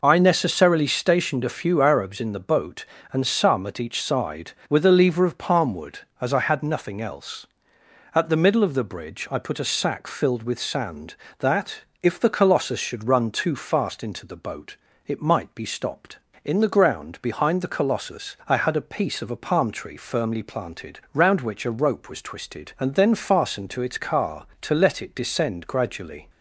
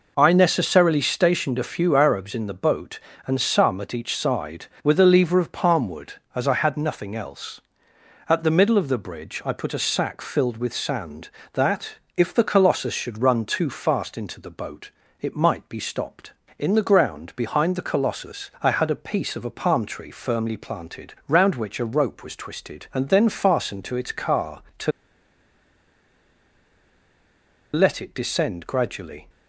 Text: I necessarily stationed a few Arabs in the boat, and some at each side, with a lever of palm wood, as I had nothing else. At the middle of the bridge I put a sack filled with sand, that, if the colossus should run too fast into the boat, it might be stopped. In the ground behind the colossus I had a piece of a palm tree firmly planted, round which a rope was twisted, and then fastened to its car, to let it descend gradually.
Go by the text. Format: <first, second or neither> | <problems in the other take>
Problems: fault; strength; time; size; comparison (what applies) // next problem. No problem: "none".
first | pauses between "to" and "let"; strong; at 24.9 s; 2.8 s long